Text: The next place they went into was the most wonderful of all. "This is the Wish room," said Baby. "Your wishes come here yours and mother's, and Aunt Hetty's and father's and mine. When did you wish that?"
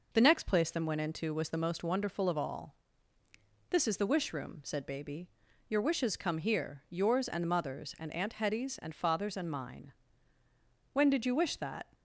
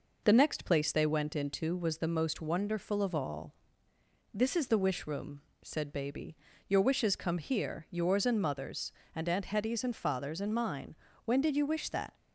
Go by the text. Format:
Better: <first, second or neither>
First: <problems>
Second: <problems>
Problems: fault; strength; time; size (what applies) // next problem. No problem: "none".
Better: second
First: says "them" for "they"; at 0.6 s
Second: none